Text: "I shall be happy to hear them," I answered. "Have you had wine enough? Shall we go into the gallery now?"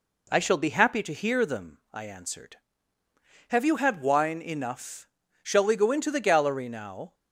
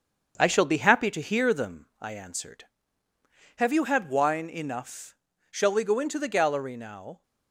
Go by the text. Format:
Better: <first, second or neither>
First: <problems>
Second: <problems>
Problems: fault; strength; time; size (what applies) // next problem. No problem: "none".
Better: first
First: none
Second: gets quieter; noticeable; throughout; 4.5 dB